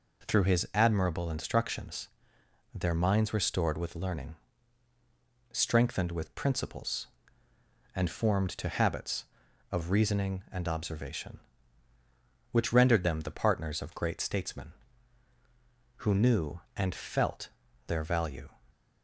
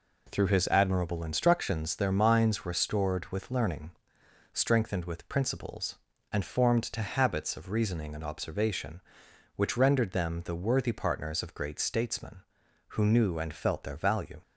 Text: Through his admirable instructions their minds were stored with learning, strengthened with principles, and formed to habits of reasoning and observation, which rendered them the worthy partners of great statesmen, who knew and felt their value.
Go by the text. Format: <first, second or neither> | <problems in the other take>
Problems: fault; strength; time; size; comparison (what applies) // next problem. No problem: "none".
second | pauses between "instructions" and "their"; noticeable; at 2.0 s; 0.66 s long // skips "worthy"; at 13.2 s // pauses between "felt" and "their"; at 17.4 s; 0.38 s long